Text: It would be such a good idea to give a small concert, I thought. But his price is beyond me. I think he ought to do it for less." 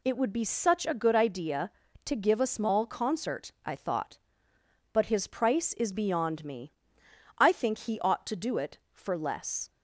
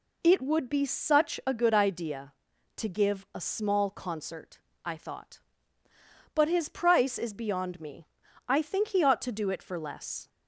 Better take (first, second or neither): neither